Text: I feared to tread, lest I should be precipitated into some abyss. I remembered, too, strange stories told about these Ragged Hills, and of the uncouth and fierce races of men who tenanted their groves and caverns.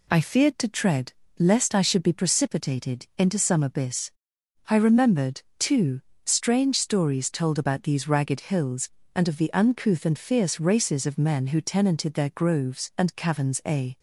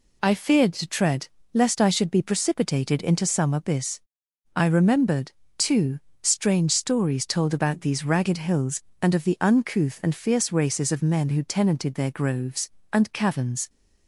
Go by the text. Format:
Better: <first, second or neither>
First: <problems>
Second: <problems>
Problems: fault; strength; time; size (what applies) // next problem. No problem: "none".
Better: second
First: goes on to say "A"; slight; from 13.6 s on; 0.32 s long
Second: none